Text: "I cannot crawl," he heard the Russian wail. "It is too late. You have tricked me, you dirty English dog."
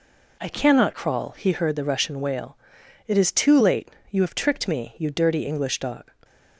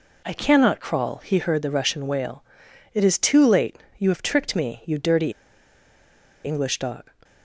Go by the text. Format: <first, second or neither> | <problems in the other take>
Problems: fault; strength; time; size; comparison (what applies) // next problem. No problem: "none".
first | pauses between "dirty" and "English"; at 5.3 s; 1.1 s long